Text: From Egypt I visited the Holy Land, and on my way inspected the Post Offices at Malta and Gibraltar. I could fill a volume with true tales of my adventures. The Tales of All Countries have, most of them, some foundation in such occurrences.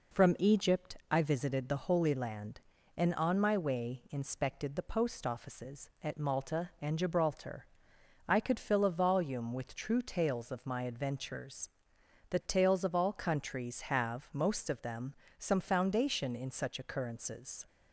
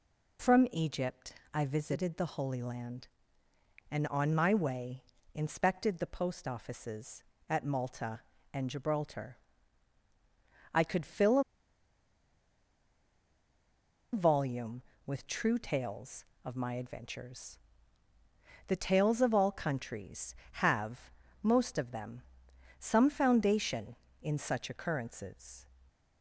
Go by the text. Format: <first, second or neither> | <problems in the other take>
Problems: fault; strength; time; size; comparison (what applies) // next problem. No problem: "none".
first | pauses between "Egypt" and "I"; slight; at 1.3 s; 0.18 s long // pauses between "way" and "inspected"; slight; at 5.0 s; 0.32 s long // pauses between "a" and "volume"; strong; at 11.4 s; 2.7 s long